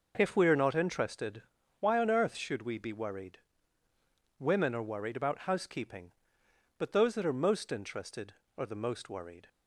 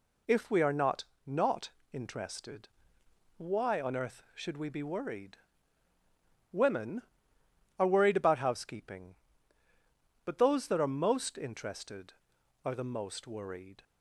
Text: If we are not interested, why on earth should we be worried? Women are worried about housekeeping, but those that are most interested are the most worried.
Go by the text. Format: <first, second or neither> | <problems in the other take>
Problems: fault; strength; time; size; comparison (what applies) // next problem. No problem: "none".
first | says "not" twice; at 1.2 s